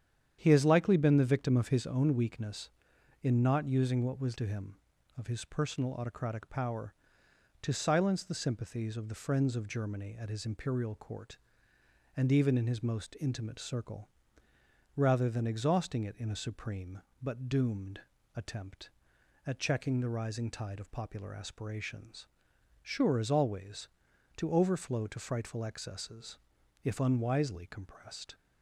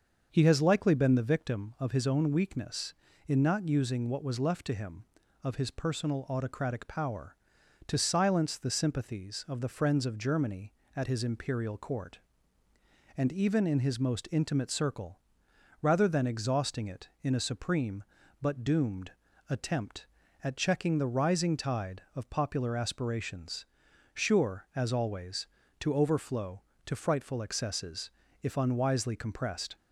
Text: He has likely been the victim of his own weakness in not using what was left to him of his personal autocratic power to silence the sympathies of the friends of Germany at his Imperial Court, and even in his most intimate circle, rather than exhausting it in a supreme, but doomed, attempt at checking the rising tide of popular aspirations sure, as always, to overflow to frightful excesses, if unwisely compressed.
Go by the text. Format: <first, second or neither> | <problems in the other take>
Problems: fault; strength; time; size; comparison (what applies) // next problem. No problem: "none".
second | starts louder than the rest; strong; until 1.4 s; 9 dB; also in the second // skips "left"; at 4.3 s // pauses between "aspirations" and "sure"; noticeable; at 22.2 s; 0.56 s long; noticeable in the second